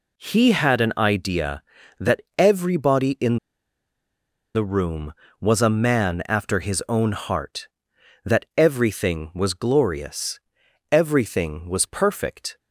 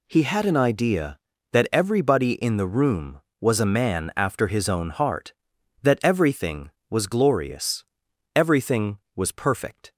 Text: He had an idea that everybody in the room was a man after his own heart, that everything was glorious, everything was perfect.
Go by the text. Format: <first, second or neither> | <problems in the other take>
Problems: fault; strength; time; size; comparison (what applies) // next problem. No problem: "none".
second | pauses between "that" and "everybody"; slight; at 2.2 s; 0.16 s long // pauses between "in" and "the"; at 3.3 s; 1.1 s long